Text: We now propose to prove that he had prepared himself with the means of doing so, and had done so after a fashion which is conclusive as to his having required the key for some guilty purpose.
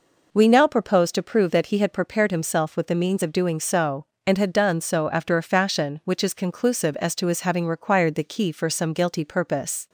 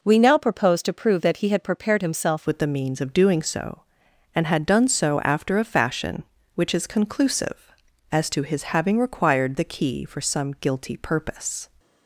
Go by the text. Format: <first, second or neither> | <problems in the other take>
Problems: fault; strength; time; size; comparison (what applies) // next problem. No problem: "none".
first | changes voice at "with"; from 2.4 s on; 9.2 s long